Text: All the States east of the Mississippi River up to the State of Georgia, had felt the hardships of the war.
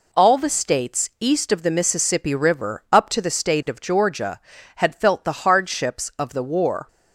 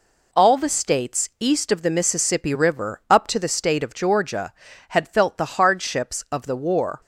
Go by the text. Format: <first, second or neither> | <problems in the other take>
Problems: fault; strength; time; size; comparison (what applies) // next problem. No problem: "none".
neither | none